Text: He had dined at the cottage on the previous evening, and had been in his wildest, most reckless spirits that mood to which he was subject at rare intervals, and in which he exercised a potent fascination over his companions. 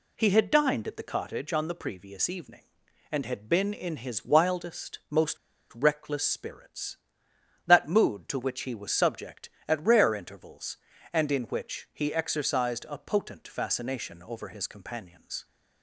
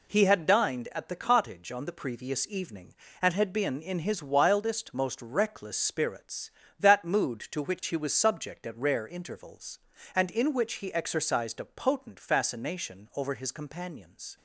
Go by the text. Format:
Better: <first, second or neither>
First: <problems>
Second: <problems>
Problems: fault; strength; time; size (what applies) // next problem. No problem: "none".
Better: second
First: pauses between "most" and "reckless"; at 5.3 s; 0.38 s long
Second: none